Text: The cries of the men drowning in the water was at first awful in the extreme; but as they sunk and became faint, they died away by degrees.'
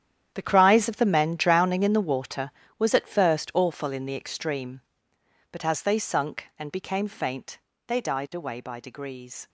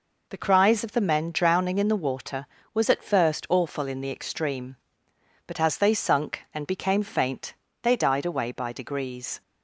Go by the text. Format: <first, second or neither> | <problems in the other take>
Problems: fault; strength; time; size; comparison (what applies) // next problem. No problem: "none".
second | gets quieter; strong; throughout; 14.5 dB